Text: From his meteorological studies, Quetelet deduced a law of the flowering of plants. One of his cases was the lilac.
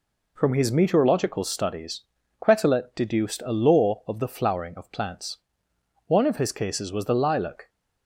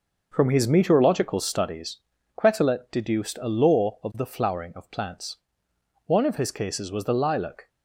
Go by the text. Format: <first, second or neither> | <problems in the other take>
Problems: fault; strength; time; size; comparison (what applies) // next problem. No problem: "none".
first | starts louder than the rest; noticeable; until 1.9 s; 5.5 dB